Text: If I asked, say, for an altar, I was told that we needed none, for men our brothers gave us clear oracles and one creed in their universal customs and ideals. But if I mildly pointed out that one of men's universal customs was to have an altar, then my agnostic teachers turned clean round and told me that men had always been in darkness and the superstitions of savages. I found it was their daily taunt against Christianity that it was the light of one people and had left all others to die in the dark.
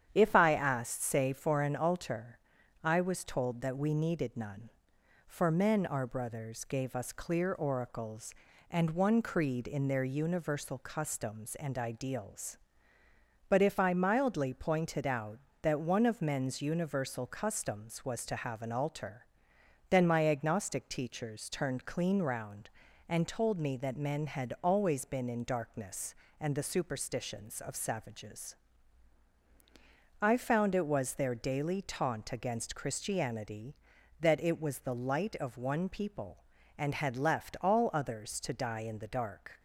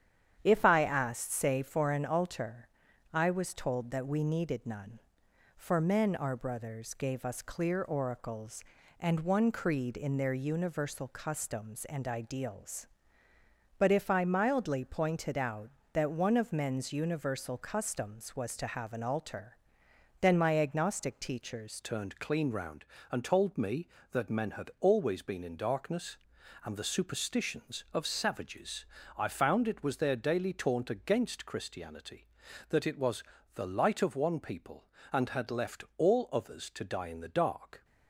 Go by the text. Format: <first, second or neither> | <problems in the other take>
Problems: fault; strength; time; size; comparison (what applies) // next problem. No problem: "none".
first | starts louder than the rest; strong; until 1.4 s; 9 dB; strong in the first // changes voice at "turned"; from 21.8 s on; 16.0 s long // pauses between "was" and "the"; slight; at 33.2 s; 0.32 s long